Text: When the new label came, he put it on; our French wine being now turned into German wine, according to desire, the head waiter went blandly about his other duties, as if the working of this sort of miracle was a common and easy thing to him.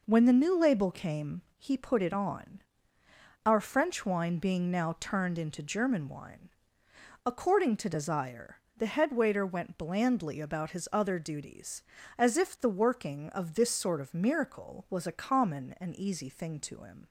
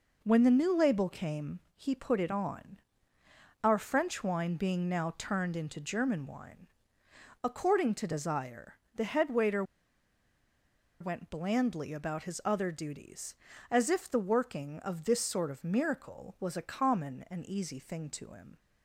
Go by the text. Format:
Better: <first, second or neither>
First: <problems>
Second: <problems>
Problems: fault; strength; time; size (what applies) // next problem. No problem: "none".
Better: first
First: none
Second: pauses between "waiter" and "went"; strong; at 9.6 s; 1.3 s long